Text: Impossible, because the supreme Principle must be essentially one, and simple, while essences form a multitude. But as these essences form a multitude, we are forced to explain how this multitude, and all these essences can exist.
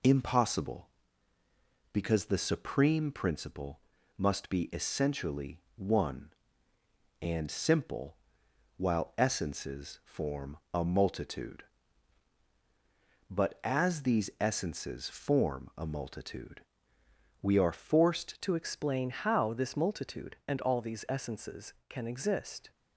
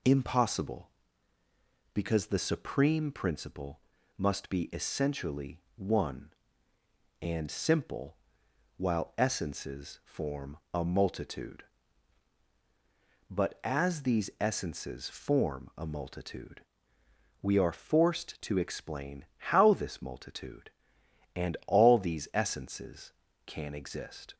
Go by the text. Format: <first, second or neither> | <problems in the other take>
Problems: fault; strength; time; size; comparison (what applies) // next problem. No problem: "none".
second | pauses between "Principle" and "must"; at 3.7 s; 0.40 s long; also in the second // pauses between "essentially" and "one"; slight; at 5.6 s; 0.16 s long; slight in the second // pauses between "form" and "a"; slight; at 10.5 s; 0.18 s long; slight in the second // changes voice at "to"; from 18.4 s on; 4.3 s long